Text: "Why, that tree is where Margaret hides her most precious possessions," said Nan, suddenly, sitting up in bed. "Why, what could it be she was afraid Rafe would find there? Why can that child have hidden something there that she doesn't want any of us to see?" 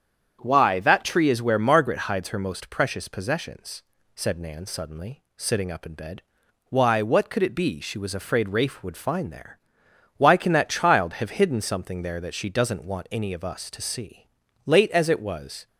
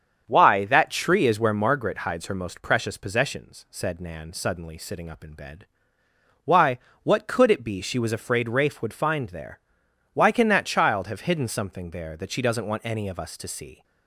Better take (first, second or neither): second